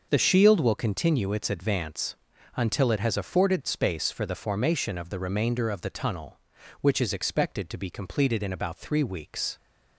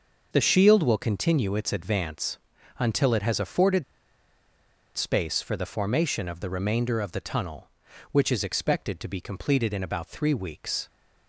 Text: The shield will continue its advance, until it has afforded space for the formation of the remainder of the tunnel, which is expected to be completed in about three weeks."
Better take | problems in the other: first | pauses between "afforded" and "space"; at 3.8 s; 1.1 s long

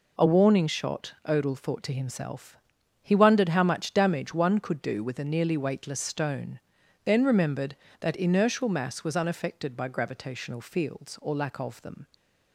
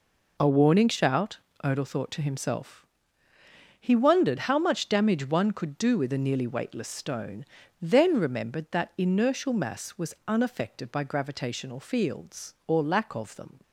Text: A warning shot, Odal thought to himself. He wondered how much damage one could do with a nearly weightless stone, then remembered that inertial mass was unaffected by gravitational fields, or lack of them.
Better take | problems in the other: first | says "shout" for "shot"; at 0.8 s

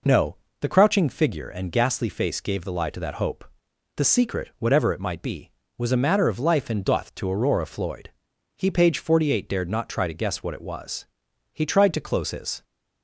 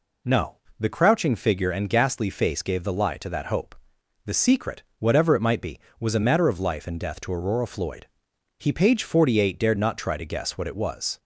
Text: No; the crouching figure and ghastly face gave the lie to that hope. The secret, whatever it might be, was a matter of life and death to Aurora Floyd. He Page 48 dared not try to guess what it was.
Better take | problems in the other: second | goes on to say "He tried to close his"; noticeable; from 11.5 s on; 1.1 s long

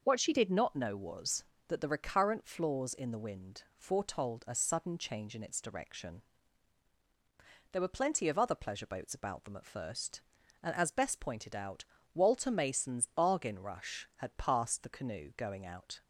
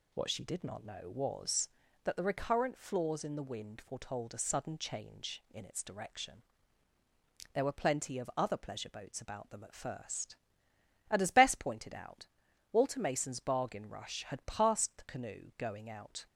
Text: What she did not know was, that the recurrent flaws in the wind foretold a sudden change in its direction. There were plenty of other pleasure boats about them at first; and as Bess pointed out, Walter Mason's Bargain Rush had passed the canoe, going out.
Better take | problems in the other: neither | none

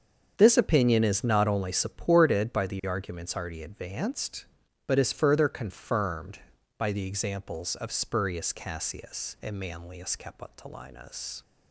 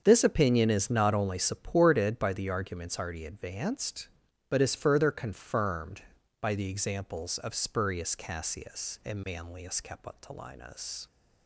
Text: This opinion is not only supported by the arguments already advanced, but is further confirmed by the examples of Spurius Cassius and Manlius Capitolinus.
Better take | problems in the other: neither | starts louder than the rest; strong; the same in both

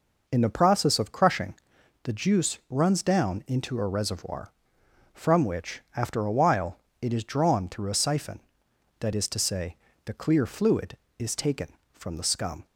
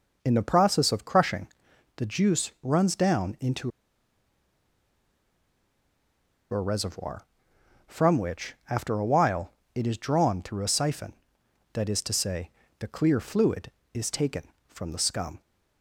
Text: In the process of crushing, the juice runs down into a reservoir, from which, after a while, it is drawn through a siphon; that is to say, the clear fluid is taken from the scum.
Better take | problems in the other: first | pauses between "into" and "a"; strong; at 3.7 s; 2.8 s long

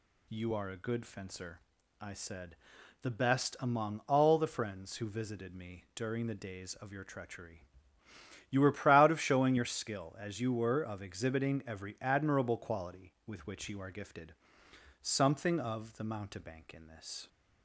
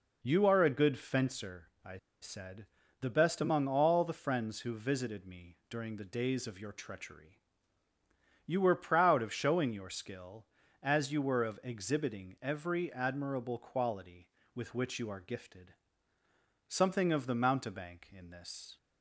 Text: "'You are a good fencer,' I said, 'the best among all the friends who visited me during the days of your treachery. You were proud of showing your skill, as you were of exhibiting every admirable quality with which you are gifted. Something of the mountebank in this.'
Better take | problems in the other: first | pauses between "I" and "said"; slight; at 1.9 s; 0.24 s long

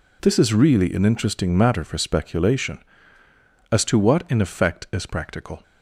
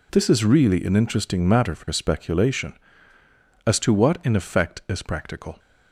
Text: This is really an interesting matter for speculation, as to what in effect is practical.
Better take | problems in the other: neither | none

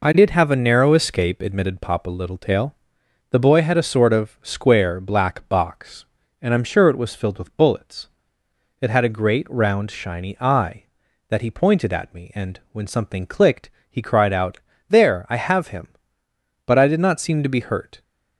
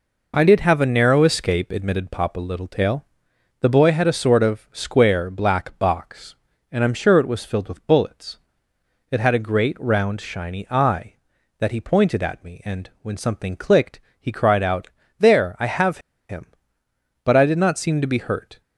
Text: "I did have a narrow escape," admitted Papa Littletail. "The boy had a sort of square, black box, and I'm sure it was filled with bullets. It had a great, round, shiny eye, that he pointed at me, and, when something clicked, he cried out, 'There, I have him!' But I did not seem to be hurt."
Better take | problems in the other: first | pauses between "have" and "him"; slight; at 15.9 s; 0.30 s long

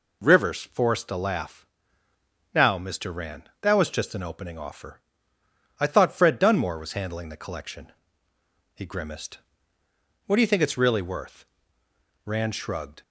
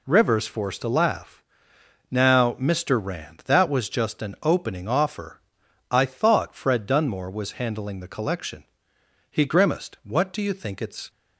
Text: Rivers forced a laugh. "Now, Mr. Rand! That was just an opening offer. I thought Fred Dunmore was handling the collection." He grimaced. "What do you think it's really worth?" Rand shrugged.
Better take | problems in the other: first | stops before "really worth Rand shrugged"; at 11.0 s

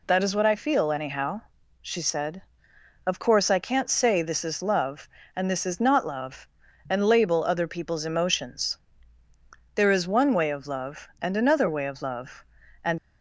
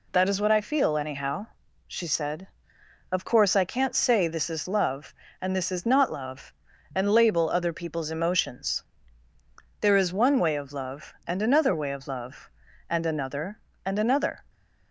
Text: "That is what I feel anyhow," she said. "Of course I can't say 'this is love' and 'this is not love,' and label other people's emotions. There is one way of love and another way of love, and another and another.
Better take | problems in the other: second | stops before "another and another"; at 12.9 s

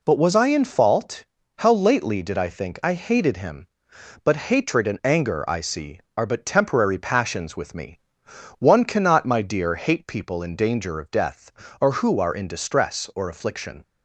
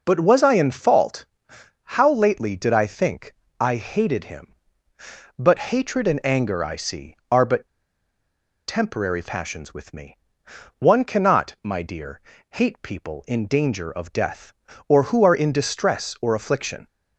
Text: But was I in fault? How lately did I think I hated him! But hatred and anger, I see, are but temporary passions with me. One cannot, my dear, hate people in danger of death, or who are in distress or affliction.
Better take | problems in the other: first | pauses between "think" and "I"; slight; at 3.3 s; 0.24 s long // pauses between "but" and "temporary"; at 7.6 s; 1.0 s long

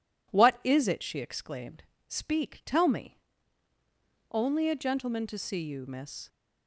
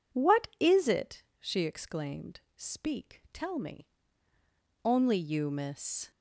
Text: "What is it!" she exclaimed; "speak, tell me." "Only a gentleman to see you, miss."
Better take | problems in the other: first | skips "a gentleman to see"; at 5.1 s

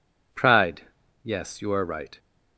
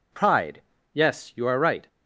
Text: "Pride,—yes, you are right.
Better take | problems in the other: neither | none

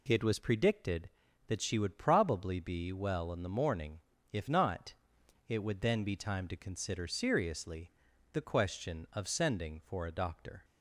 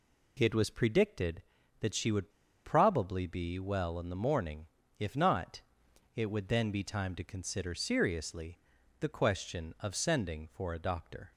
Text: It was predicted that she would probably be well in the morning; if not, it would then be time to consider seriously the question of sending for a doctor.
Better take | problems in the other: first | pauses between "would" and "probably"; slight; at 2.2 s; 0.35 s long // pauses between "seriously" and "the"; at 8.5 s; 0.44 s long; also in the first

